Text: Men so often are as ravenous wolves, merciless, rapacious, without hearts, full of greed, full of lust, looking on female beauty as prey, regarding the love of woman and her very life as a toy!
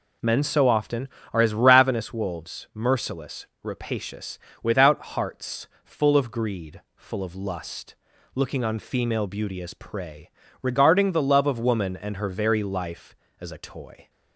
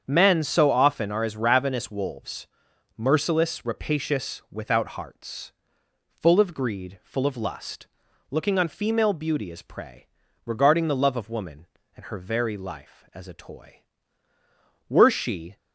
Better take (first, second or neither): first